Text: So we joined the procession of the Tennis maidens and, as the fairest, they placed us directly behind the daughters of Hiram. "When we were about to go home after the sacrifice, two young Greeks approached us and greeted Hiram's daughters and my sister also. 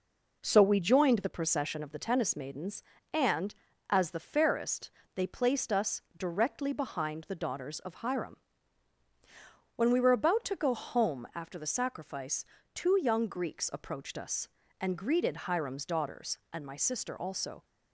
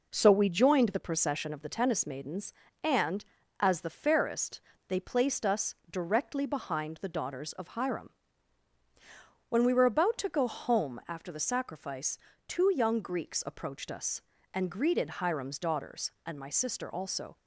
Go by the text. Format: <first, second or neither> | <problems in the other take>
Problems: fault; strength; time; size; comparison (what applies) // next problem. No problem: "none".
neither | none